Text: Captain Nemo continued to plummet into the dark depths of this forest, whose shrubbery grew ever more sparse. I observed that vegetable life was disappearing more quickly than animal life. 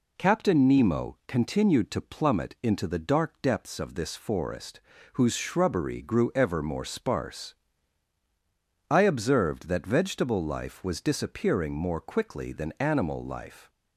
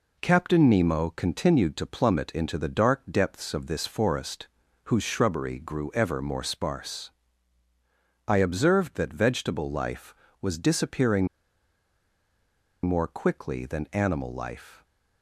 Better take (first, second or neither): first